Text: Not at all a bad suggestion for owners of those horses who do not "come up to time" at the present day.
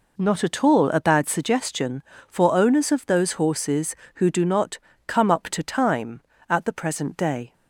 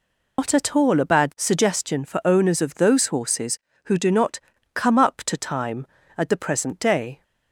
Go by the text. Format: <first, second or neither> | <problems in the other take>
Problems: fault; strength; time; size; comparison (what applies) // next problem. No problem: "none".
first | loses the start of "Not"; at 0.3 s; 135 ms // pauses between "not" and "come"; slight; at 4.3 s; 0.34 s long; slight in the first